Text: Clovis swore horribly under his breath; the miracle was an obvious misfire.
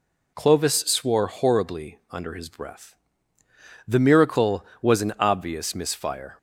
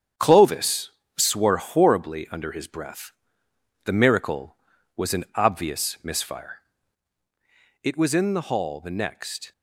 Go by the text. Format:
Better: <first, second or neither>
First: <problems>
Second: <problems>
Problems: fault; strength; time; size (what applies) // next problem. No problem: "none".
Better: first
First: none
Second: starts louder than the rest; strong; until 1.4 s; 8 dB // pauses between "Clovis" and "swore"; slight; at 0.9 s; 0.26 s long // goes on to say "It was in the hall the next"; strong; from 7.8 s on; 1.6 s long